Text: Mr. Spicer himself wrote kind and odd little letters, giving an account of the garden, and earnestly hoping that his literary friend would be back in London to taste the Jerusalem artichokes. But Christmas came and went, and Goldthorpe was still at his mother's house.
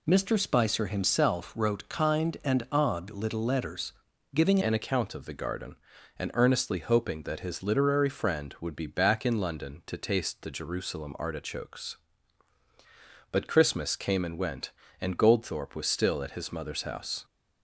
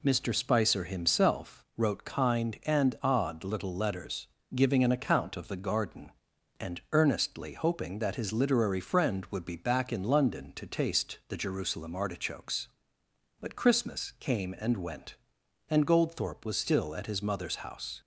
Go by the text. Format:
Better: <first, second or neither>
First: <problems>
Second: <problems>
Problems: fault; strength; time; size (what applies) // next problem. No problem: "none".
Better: second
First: changes voice at "an"; from 4.6 s on; 12.6 s long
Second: none